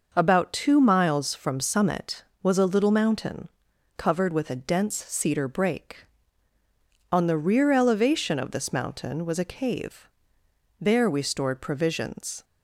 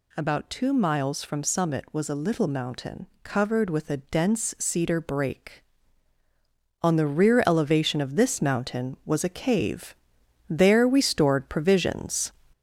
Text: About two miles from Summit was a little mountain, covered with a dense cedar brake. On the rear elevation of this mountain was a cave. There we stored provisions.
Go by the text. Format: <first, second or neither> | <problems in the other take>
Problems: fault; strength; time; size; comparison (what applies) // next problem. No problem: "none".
first | gets louder; slight; throughout; 3.5 dB